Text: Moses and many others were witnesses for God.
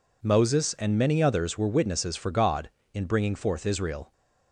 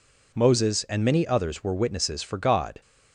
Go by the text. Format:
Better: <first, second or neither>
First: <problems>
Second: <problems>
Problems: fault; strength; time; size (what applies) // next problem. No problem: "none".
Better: second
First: goes on to say "In bringing forth Israel"; noticeable; from 2.9 s on; 1.1 s long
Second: none